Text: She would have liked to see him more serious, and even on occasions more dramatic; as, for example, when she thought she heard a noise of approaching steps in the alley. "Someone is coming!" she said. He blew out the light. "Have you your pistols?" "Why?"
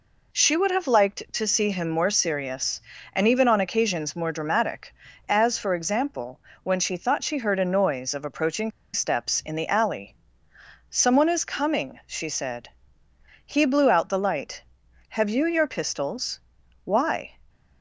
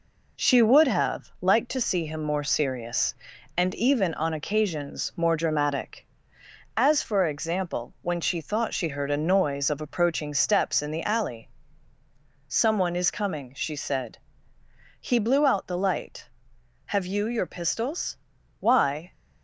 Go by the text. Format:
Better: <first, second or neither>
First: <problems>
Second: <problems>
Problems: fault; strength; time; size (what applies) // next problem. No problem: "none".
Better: second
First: pauses between "approaching" and "steps"; slight; at 8.7 s; 0.23 s long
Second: none